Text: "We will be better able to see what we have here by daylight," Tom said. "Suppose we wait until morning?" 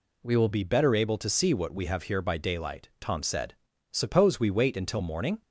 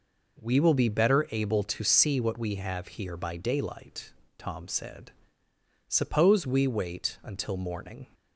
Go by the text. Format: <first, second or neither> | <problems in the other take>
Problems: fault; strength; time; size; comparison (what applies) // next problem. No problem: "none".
second | changes voice at "be"; from 0.5 s on; 4.9 s long